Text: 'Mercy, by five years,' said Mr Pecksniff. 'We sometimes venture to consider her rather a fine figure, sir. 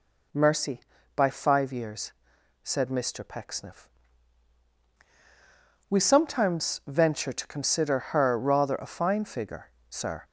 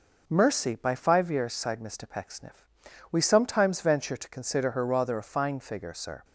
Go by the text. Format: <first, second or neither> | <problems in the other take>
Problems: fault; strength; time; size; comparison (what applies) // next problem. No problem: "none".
first | says "sighed" for "said"; at 1.5 s